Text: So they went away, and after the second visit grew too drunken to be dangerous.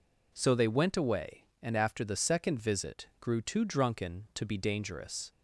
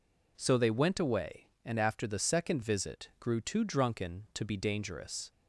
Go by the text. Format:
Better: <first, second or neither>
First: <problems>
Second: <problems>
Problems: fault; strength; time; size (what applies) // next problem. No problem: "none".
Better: neither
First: none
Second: none